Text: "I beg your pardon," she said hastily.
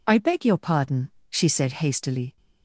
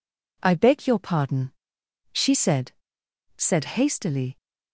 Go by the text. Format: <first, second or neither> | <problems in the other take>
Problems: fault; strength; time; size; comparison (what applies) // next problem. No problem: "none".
first | says "said" twice; at 3.3 s